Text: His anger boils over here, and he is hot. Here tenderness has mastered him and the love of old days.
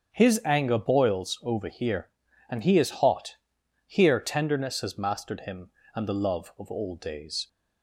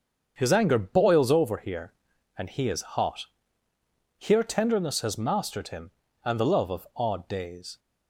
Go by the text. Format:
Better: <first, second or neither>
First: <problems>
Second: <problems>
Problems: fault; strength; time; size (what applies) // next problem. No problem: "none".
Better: first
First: starts louder than the rest; strong; until 1.1 s; 7 dB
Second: starts louder than the rest; until 1.3 s; 7 dB // says "odd" for "old"; at 6.9 s